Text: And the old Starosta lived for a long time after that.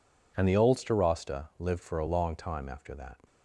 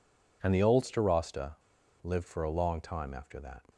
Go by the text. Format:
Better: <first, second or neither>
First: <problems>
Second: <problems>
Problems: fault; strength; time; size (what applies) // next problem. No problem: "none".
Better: first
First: none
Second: pauses between "Starosta" and "lived"; noticeable; at 1.5 s; 0.49 s long